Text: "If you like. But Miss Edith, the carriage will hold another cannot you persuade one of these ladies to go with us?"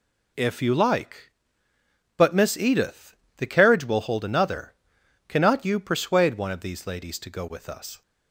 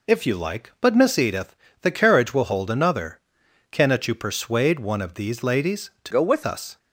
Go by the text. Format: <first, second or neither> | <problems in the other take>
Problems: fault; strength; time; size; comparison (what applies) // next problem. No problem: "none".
first | pauses between "another" and "cannot"; noticeable; at 3.1 s; 0.50 s long; noticeable in the first // changes voice from "go" to "with"; from 6.1 to 6.4 s; 0.3 s long